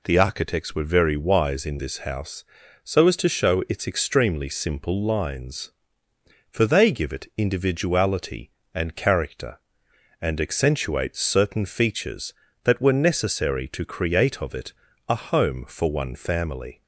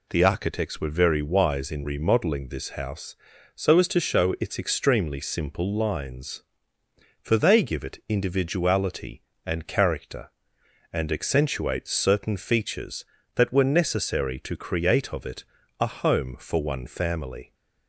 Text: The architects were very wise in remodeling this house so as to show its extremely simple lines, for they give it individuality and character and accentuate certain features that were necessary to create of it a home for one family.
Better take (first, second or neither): second